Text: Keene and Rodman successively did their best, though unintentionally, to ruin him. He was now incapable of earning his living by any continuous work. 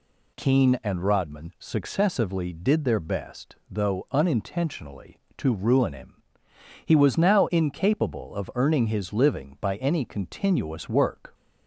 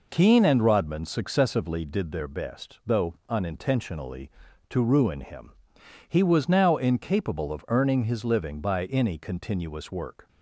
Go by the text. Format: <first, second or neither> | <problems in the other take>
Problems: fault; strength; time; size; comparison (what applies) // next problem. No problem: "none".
neither | none